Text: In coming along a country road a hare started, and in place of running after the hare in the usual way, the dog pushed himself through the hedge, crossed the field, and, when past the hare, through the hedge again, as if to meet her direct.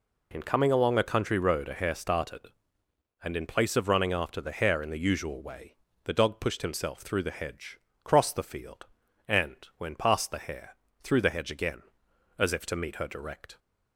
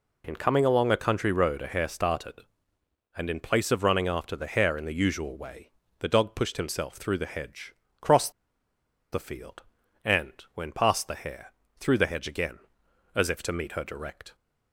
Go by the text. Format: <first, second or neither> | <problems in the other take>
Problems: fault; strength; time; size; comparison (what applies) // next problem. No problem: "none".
first | pauses between "crossed" and "the"; noticeable; at 8.3 s; 0.81 s long